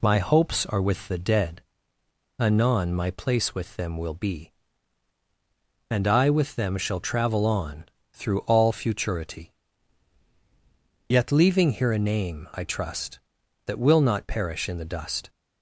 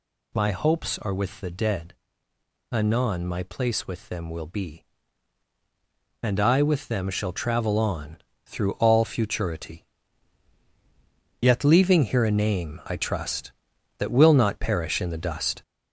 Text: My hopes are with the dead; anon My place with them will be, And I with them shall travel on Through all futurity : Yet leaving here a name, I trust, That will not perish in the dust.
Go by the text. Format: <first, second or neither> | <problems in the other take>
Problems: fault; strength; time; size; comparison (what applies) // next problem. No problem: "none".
first | gets louder; noticeable; throughout; 5 dB // pauses between "on" and "Through"; slight; at 8.1 s; 0.26 s long; slight in the first